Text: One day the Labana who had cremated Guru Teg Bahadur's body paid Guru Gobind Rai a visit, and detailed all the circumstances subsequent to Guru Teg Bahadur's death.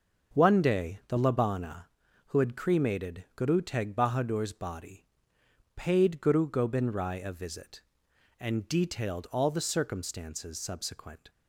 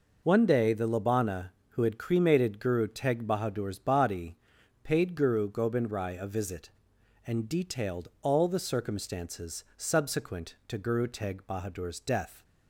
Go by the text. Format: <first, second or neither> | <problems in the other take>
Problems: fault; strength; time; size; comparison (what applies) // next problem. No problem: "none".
second | pauses between "body" and "paid"; noticeable; at 5.0 s; 0.72 s long; noticeable in the second // stops before "to Guru Teg Bahadur's death"; at 11.2 s